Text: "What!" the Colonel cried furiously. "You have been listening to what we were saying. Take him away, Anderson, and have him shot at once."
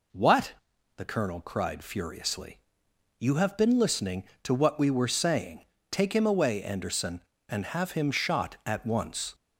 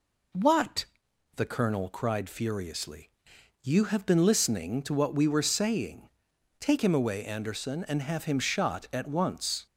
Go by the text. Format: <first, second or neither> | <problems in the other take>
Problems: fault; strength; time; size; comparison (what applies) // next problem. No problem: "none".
neither | none